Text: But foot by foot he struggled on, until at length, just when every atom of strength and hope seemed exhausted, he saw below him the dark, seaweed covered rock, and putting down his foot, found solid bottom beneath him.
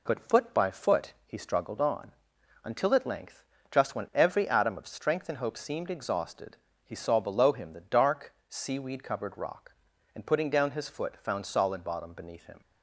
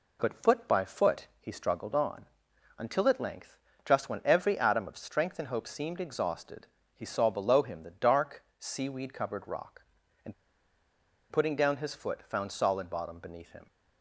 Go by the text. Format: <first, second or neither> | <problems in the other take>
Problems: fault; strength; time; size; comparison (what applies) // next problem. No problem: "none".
first | pauses between "and" and "putting"; at 10.3 s; 0.98 s long